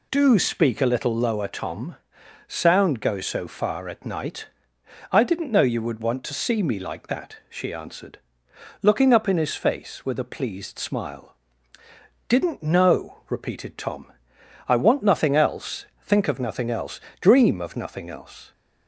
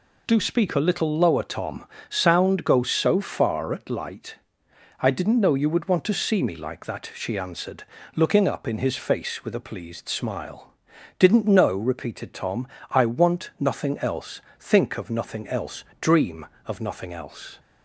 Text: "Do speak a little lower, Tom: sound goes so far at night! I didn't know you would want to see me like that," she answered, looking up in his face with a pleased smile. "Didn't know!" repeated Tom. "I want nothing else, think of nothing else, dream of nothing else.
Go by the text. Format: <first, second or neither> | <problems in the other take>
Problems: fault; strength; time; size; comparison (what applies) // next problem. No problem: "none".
first | says "light" for "night"; at 3.9 s